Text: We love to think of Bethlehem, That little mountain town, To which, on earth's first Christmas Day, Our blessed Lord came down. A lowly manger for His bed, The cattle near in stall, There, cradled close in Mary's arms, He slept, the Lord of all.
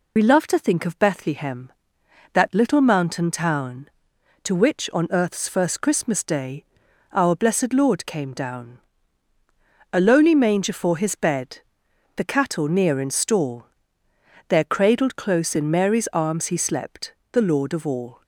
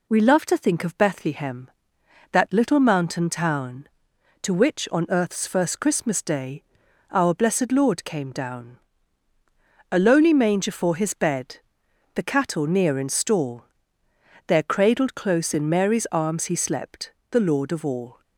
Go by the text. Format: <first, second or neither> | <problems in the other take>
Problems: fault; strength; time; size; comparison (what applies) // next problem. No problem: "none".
second | loses the start of "We"; at 0.1 s; 50 ms